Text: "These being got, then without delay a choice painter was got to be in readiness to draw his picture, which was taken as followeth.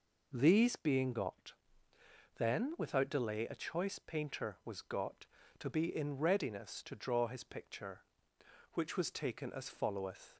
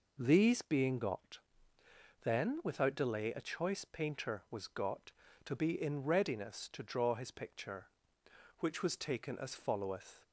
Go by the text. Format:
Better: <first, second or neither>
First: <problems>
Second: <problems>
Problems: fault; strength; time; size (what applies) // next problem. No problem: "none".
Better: neither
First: none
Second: none